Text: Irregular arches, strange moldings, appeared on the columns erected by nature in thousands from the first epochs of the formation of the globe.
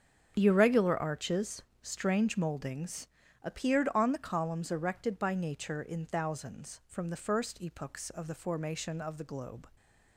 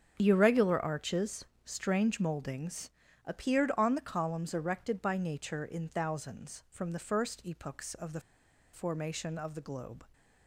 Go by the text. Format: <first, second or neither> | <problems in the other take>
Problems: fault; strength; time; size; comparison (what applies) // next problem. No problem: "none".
first | starts louder than the rest; strong; until 1.2 s; 7.5 dB; strong in the first // pauses between "the" and "formation"; noticeable; at 8.2 s; 0.53 s long